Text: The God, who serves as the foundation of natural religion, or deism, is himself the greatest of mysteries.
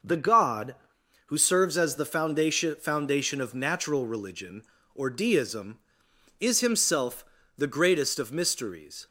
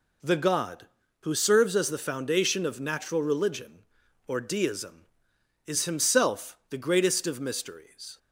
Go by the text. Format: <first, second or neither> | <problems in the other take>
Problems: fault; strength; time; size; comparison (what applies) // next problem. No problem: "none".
second | says "foundation" twice; at 2.7 s // pauses between "himself" and "the"; slight; at 7.2 s; 0.32 s long